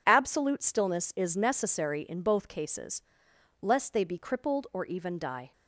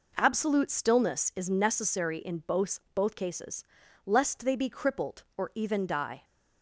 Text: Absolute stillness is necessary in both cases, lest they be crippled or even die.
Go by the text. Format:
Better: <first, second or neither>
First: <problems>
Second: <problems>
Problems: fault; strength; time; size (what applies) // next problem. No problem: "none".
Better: first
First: none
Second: says "both" twice; at 2.9 s